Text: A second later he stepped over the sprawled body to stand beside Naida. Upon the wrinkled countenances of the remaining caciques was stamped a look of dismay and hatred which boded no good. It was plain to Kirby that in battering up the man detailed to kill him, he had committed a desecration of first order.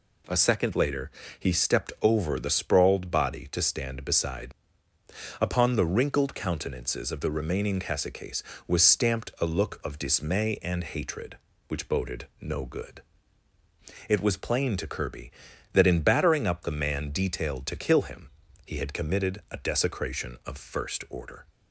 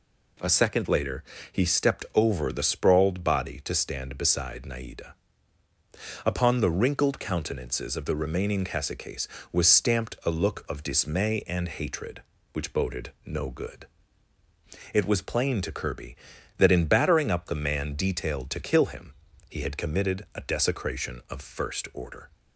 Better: second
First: pauses between "later" and "he"; slight; at 1.0 s; 0.28 s long // skips "Naida"; at 4.9 s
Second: pauses between "later" and "he"; slight; at 1.2 s; 0.28 s long

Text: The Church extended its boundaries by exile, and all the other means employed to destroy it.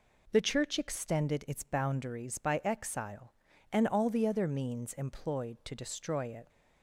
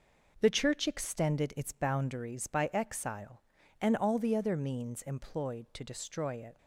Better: first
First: none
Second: gets quieter; throughout; 6.5 dB

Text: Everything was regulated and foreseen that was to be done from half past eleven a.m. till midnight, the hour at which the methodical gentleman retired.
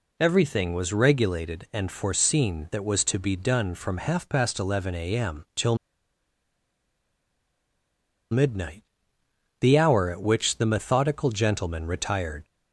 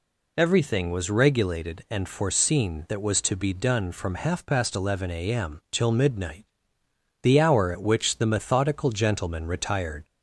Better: second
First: pauses between "till" and "midnight"; strong; at 5.7 s; 2.5 s long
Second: none

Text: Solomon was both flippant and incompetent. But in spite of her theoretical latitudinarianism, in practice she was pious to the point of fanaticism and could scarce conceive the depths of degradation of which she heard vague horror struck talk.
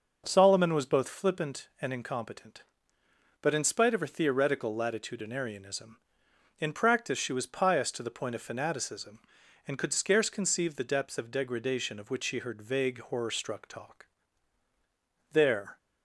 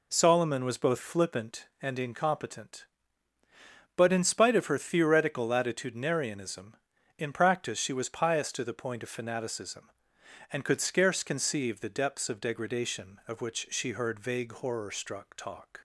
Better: second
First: goes on to say "There"; slight; from 15.3 s on; 0.44 s long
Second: none

